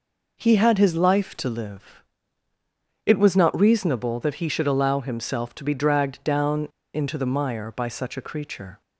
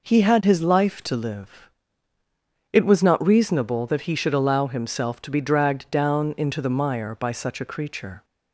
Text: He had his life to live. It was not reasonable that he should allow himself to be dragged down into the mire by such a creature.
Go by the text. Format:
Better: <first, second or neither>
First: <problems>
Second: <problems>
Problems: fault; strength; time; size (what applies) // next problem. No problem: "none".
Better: second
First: pauses between "down" and "into"; slight; at 6.6 s; 0.26 s long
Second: none